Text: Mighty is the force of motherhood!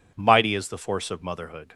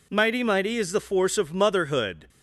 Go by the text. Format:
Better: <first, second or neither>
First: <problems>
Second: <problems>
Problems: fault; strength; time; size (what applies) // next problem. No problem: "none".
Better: first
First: none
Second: says "Mighty" twice; at 0.4 s